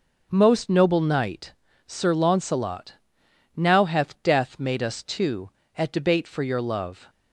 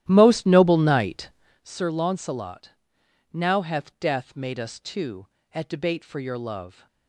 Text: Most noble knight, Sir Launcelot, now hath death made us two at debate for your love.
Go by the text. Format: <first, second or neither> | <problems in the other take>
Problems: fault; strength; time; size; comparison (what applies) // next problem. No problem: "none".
first | starts louder than the rest; strong; until 1.6 s; 12.5 dB